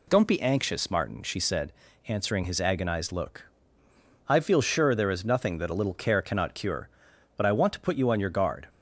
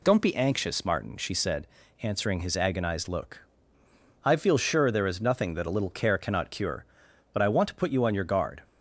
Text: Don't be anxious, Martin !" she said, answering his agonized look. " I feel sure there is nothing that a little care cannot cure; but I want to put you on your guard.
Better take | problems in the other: neither | none

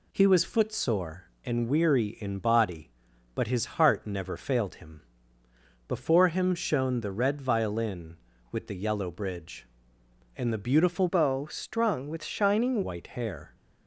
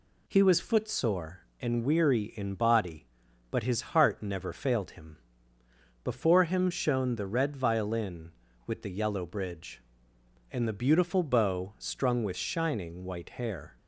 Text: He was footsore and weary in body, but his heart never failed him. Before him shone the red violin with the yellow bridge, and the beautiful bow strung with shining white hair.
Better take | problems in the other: second | changes voice from "bow" to "shining"; from 11.0 to 12.8 s; 1.8 s long

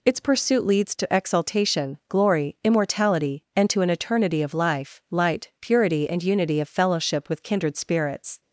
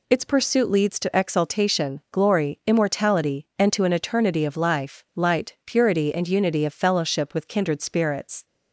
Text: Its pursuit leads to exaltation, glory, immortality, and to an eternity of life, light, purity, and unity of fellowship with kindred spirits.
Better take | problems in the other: neither | none

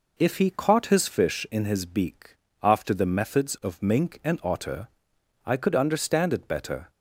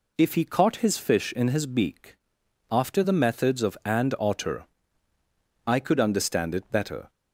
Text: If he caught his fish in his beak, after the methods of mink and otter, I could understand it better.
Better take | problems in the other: first | skips "mink"; at 3.8 s

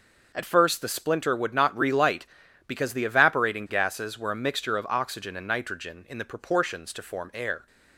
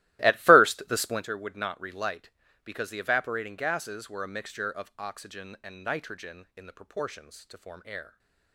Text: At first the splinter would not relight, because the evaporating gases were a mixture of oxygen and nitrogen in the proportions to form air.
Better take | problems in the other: first | starts louder than the rest; strong; until 1.2 s; 16.5 dB

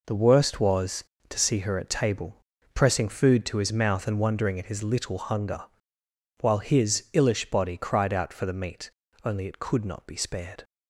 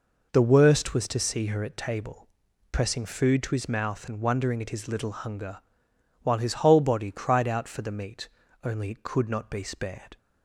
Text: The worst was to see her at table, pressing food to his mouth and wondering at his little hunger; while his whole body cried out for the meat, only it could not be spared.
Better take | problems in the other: second | says "illish" for "whole"; at 7.1 s

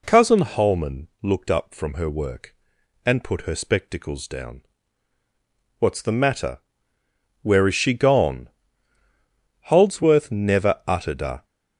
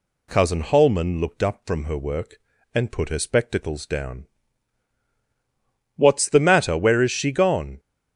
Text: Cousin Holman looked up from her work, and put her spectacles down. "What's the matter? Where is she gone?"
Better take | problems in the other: second | pauses between "Holman" and "looked"; slight; at 1.0 s; 0.16 s long // goes on to say "Holdsworth never uttered a"; strong; from 9.6 s on; 1.7 s long

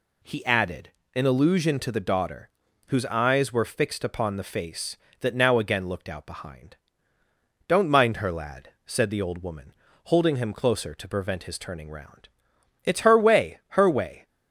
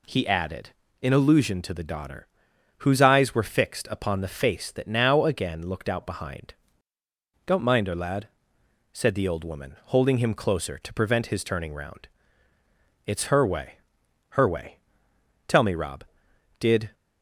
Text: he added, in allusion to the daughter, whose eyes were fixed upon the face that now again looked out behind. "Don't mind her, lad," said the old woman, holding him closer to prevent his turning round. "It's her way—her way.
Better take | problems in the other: first | goes on to say "Tell me Rob Did"; from 15.4 s on; 1.4 s long

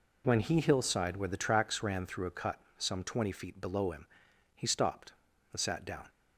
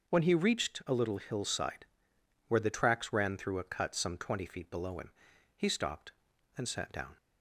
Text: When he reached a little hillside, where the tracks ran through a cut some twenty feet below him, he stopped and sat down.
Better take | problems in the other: second | skips "reached a little"; at 0.5 s // pauses between "cut" and "some"; slight; at 2.5 s; 0.22 s long

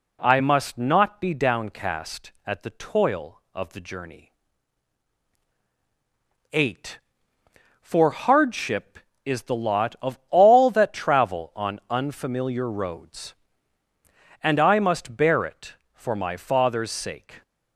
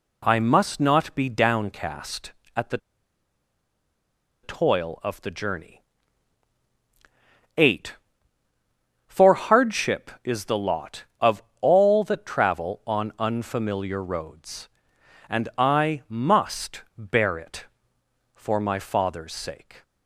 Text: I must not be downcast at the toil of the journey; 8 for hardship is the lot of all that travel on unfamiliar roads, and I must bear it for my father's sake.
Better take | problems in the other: first | pauses between "the" and "toil"; strong; at 2.7 s; 1.6 s long // pauses between "of" and "all"; slight; at 11.4 s; 0.20 s long // pauses between "must" and "bear"; slight; at 16.8 s; 0.16 s long

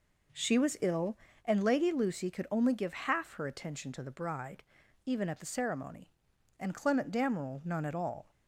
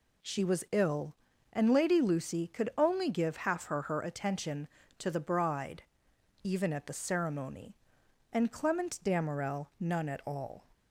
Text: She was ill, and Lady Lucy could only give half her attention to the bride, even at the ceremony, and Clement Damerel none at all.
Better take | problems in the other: first | says "her" twice; at 3.8 s

